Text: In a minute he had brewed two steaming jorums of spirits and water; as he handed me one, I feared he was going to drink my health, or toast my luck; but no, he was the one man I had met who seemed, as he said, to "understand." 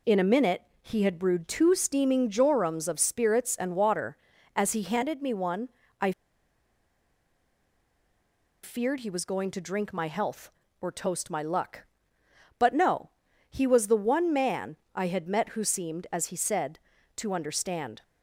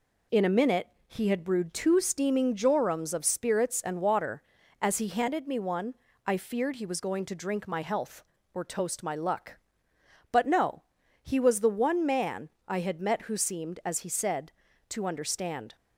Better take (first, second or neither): second